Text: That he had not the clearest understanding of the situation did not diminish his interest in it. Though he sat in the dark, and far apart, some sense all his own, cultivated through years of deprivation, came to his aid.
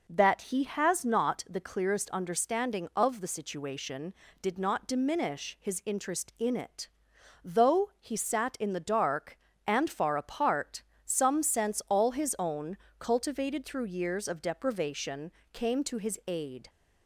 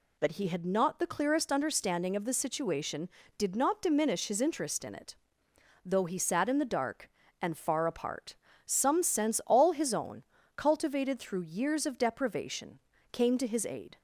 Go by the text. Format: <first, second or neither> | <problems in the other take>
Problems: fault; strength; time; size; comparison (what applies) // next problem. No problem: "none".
second | says "has" for "had"; at 0.6 s